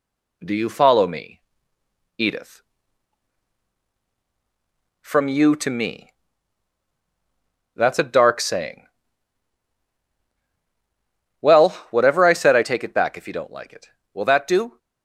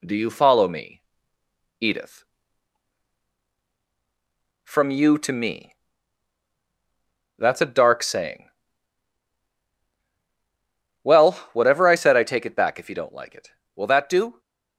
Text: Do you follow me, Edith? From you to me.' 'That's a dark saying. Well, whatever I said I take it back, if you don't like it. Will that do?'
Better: neither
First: none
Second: none

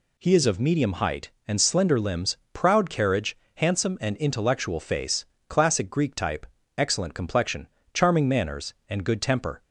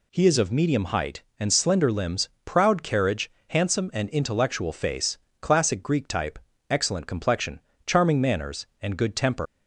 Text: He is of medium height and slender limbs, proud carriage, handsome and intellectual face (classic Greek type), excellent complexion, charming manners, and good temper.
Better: first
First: none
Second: leaves "temper" unfinished; at 9.4 s; 120 ms

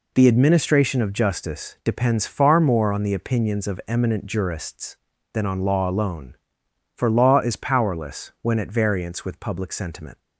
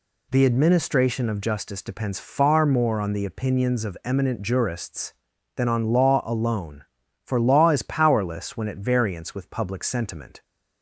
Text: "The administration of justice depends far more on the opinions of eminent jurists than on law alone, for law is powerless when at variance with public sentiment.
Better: neither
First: none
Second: none

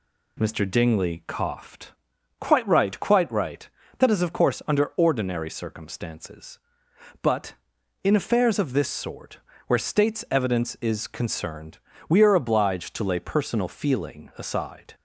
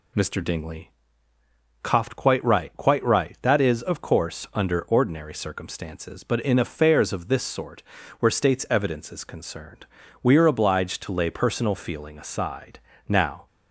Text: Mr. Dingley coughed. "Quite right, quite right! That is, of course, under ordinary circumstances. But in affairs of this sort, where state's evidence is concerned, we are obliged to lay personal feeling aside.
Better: first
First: none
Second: pauses between "Dingley" and "coughed"; noticeable; at 0.9 s; 0.92 s long // goes on to say "Now"; slight; from 13.0 s on; 0.38 s long

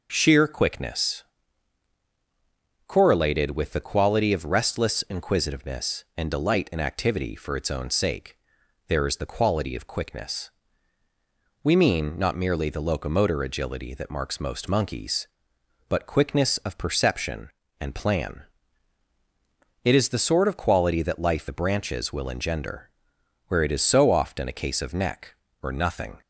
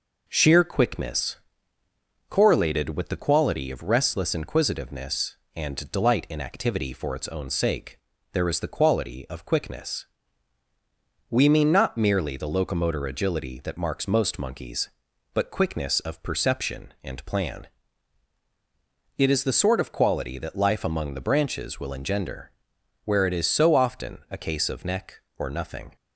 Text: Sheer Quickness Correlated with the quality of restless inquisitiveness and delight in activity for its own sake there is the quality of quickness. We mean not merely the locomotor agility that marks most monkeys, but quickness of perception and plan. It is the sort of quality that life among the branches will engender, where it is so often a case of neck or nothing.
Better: second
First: pauses between "Quickness" and "Correlated"; strong; at 1.2 s; 1.6 s long // pauses between "sake" and "there"; noticeable; at 8.3 s; 0.54 s long // skips "among"; at 21.4 s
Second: pauses between "Quickness" and "Correlated"; noticeable; at 1.3 s; 0.92 s long // pauses between "sake" and "there"; slight; at 7.9 s; 0.34 s long

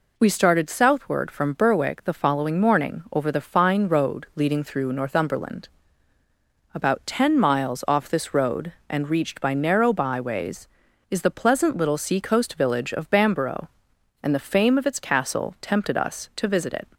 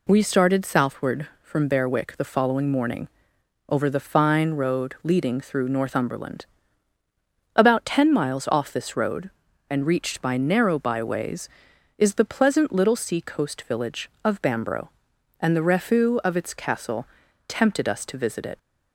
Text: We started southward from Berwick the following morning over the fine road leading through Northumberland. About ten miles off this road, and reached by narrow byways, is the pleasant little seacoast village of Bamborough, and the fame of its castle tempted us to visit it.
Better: first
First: none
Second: pauses between "morning" and "over"; noticeable; at 3.0 s; 0.58 s long // says "refu" for "fame"; at 15.6 s // pauses between "castle" and "tempted"; at 17.0 s; 0.42 s long

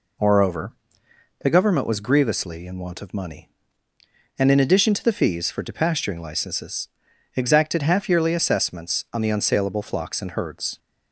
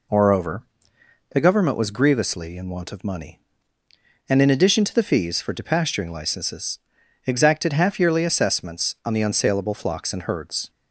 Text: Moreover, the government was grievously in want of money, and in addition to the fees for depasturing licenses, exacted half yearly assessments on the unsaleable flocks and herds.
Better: neither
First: none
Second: none

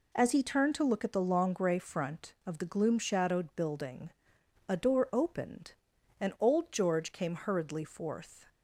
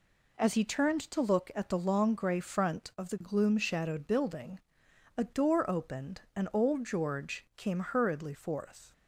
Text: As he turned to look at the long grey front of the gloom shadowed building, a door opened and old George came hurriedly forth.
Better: neither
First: none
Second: none

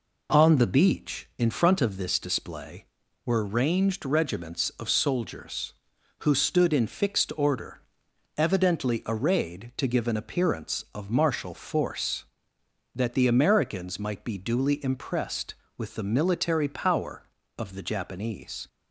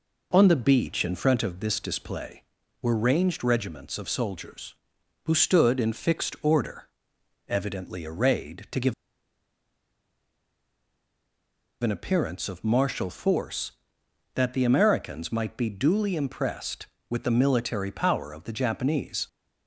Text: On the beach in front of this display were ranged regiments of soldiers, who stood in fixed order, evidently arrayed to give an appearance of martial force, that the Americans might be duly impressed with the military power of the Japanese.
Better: first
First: none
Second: pauses between "give" and "an"; strong; at 8.9 s; 2.8 s long

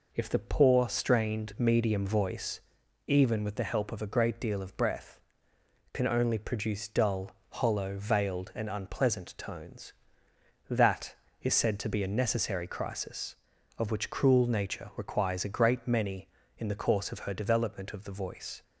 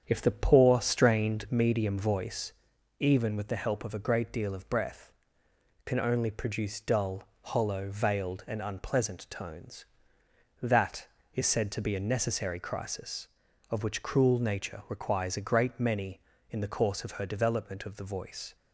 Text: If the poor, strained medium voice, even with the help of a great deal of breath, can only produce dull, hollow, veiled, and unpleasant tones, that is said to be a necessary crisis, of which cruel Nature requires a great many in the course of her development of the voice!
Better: first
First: none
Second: starts louder than the rest; strong; until 1.6 s; 7.5 dB

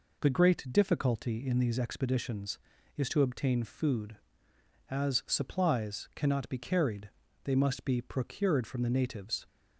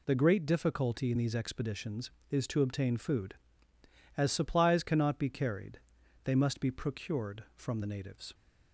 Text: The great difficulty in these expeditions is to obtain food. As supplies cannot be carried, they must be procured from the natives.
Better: neither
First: none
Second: none

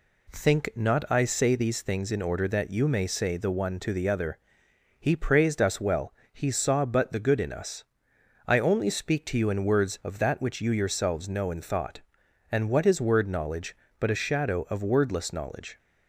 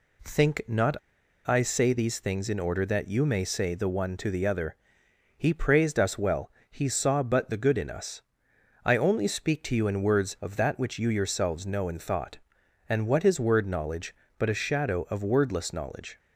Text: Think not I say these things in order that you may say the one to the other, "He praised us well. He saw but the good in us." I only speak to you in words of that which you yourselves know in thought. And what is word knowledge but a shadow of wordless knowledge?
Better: first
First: none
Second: pauses between "not" and "I"; noticeable; at 0.9 s; 0.48 s long

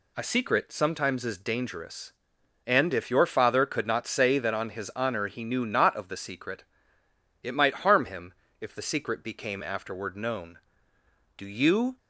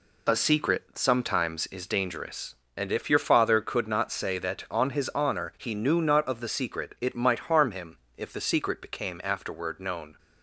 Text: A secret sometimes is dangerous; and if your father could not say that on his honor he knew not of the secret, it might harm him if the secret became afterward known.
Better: second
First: pauses between "him" and "if"; slight; at 8.3 s; 0.26 s long // goes on to say "Do you"; from 11.3 s on; 0.60 s long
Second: pauses between "him" and "if"; slight; at 7.9 s; 0.22 s long

